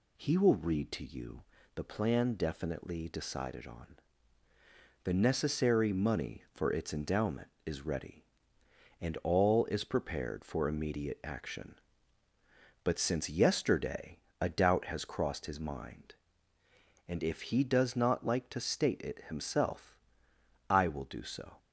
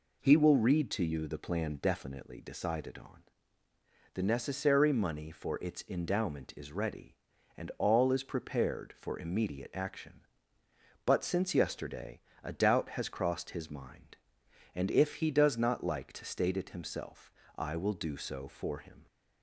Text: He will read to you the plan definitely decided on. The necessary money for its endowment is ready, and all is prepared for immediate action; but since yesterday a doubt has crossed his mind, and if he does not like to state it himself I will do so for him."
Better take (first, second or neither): second